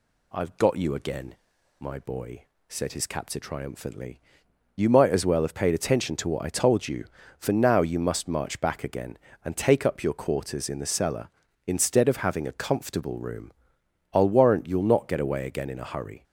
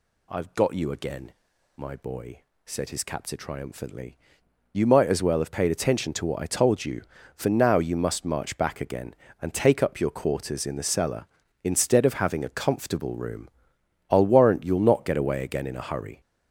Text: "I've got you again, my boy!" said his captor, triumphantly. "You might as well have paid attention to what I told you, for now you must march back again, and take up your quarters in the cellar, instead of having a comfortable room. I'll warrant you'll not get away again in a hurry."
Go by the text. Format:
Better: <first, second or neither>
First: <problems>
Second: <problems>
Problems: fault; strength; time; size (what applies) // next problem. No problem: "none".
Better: first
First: none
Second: gets louder; strong; throughout; 7.5 dB